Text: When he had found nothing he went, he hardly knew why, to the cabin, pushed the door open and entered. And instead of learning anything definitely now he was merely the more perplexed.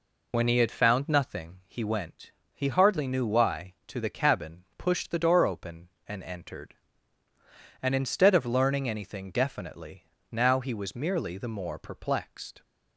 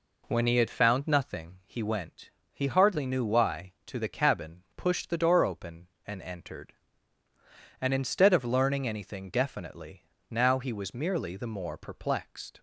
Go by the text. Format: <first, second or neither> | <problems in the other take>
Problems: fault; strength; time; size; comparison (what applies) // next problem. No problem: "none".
second | loses the start of "When"; at 0.3 s; 90 ms // pauses between "definitely" and "now"; slight; at 10.0 s; 0.24 s long; slight in the second